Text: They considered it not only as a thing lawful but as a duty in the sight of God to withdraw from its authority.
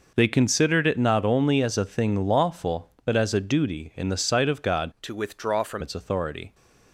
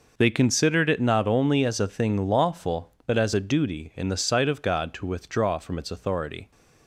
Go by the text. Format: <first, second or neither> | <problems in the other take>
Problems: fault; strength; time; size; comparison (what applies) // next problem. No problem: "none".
second | changes voice from "to" to "from"; from 5.0 to 5.8 s; 0.8 s long